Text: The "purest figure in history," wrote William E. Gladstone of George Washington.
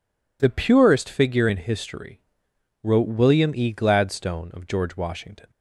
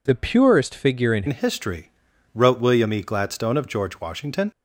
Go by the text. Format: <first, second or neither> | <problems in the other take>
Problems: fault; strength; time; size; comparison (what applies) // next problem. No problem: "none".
first | changes voice at "history"; from 1.2 s on; 3.3 s long